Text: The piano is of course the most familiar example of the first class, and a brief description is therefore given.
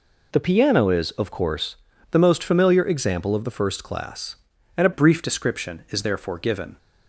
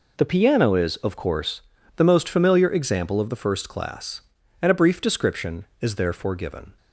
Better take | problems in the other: second | pauses between "course" and "the"; slight; at 1.7 s; 0.36 s long; slight in the second // changes voice at "brief"; from 4.9 s on; 1.8 s long

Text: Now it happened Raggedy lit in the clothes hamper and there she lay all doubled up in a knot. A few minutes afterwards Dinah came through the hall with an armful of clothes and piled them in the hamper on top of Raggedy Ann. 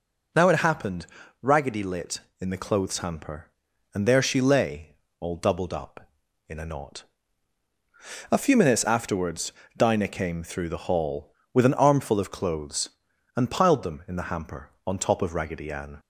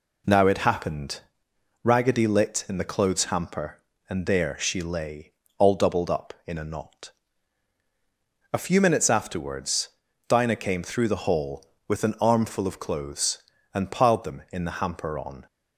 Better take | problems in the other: first | pauses between "happened" and "Raggedy"; noticeable; at 1.2 s; 0.62 s long; slight in the first // pauses between "lay" and "all"; slight; at 5.3 s; 0.26 s long; slight in the first // pauses between "afterwards" and "Dinah"; at 9.8 s; 0.38 s long; slight in the first // stops before "top of Raggedy Ann"; at 15.4 s

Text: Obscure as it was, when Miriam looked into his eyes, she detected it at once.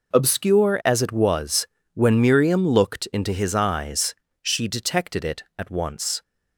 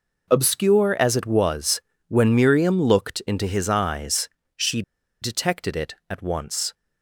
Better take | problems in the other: first | pauses between "she" and "detected"; at 4.8 s; 0.39 s long

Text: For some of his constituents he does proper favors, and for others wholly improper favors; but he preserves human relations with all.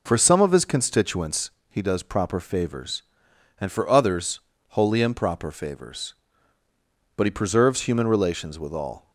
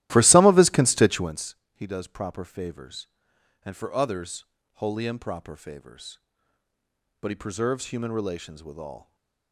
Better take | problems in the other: first | starts louder than the rest; strong; until 1.4 s; 15 dB // pauses between "constituents" and "he"; slight; at 1.5 s; 0.18 s long; slight in the first // pauses between "others" and "wholly"; slight; at 4.4 s; 0.30 s long; slight in the first // stays silent after the last word; slight; from 8.9 s on; 0.6 s long

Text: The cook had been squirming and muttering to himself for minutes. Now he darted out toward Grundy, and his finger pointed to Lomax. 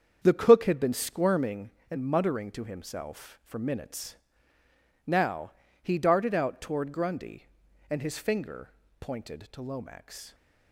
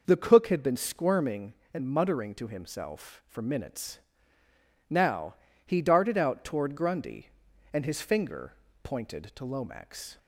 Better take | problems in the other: second | gets quieter; strong; throughout; 8.5 dB // pauses between "Now" and "he"; slight; at 5.5 s; 0.32 s long; slight in the second // pauses between "finger" and "pointed"; slight; at 8.6 s; 0.32 s long; slight in the second

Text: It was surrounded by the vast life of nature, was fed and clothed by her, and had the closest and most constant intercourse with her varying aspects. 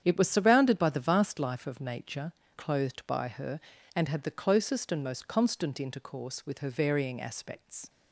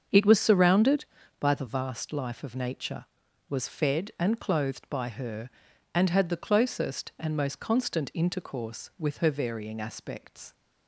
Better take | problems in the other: second | starts louder than the rest; strong; until 1.0 s; 8.5 dB; also in the second // skips "was fed and"; at 2.4 s

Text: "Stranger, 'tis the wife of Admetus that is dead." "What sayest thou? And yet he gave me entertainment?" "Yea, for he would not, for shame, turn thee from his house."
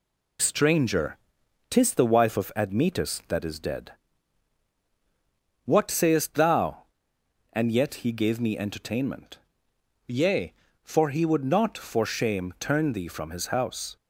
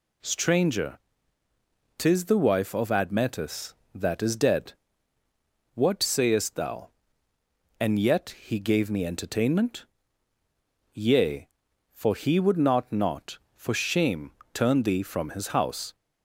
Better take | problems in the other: first | says "not" twice; at 12.9 s

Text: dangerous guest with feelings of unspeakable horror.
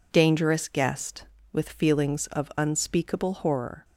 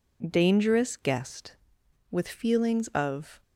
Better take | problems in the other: first | stops before "unspeakable horror"; at 3.4 s

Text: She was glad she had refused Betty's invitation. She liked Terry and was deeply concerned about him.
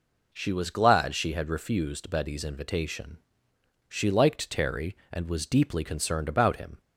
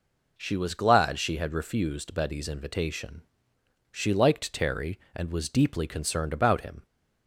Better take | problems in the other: neither | none

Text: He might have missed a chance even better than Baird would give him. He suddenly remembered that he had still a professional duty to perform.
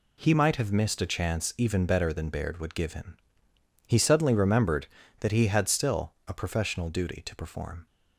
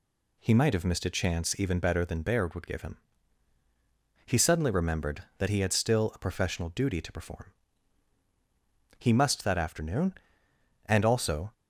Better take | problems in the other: first | goes on to say "He must that afternoon and also"; strong; from 8.9 s on; 2.5 s long

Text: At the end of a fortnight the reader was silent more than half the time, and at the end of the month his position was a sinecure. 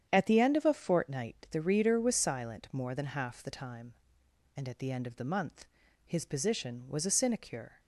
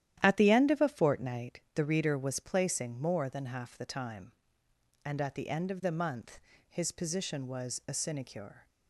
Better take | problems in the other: first | starts louder than the rest; strong; until 1.2 s; 11.5 dB; strong in the first // says "placing" for "silent"; at 2.4 s // pauses between "month" and "his"; slight; at 6.3 s; 0.30 s long; slight in the first

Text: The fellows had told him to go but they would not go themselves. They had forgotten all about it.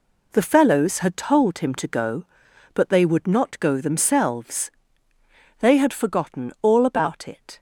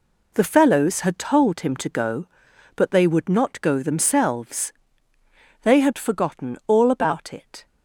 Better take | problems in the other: neither | none

